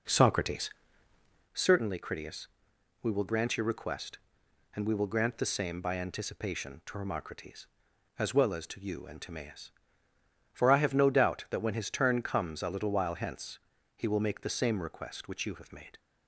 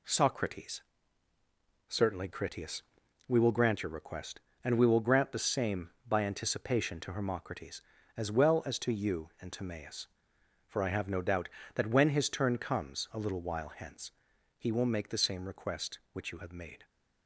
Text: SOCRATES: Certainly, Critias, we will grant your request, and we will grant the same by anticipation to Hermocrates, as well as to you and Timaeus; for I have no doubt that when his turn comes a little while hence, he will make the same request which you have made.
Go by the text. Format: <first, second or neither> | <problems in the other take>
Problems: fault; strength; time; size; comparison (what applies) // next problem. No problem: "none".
second | starts louder than the rest; noticeable; until 1.6 s; 4 dB